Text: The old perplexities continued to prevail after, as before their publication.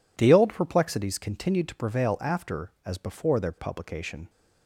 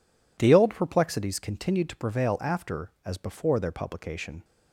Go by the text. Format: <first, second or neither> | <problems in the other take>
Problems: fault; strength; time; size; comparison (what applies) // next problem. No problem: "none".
neither | none